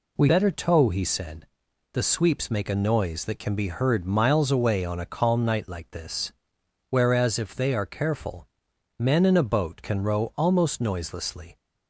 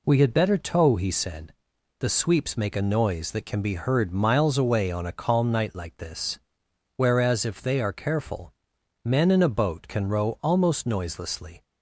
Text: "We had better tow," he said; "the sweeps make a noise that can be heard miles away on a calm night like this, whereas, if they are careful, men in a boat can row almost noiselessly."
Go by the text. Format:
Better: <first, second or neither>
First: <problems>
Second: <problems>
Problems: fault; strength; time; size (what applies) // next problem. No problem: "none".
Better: second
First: skips "had"; at 0.2 s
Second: none